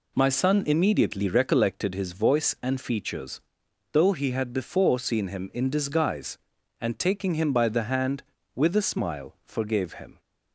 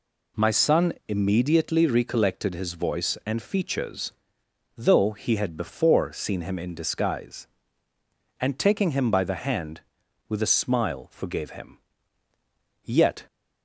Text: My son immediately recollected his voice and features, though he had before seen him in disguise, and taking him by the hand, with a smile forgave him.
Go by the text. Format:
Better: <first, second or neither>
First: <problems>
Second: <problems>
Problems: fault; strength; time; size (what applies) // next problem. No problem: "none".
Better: first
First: none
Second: goes on to say "Yet"; slight; from 12.8 s on; 0.44 s long